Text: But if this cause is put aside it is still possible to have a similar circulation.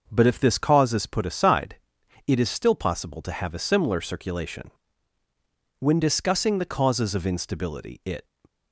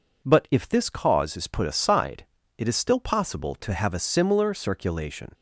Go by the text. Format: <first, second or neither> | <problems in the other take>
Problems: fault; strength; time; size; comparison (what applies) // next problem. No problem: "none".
second | pauses between "aside" and "it"; noticeable; at 1.7 s; 0.50 s long; slight in the second // goes on to say "When discussing the causes of instability it"; strong; from 5.7 s on; 2.4 s long